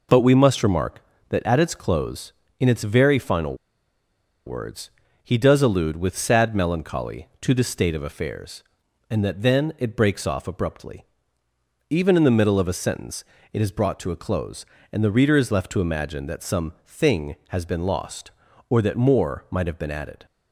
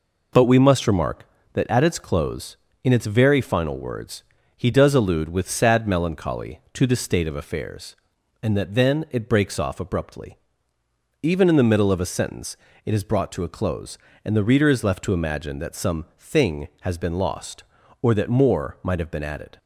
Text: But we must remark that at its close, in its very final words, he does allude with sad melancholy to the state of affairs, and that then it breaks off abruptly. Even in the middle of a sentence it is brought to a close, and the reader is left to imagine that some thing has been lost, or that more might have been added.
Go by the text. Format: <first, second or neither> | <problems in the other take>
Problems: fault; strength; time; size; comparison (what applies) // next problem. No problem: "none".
second | pauses between "final" and "words"; noticeable; at 3.5 s; 0.92 s long // pauses between "sentence" and "it"; slight; at 13.2 s; 0.30 s long; slight in the second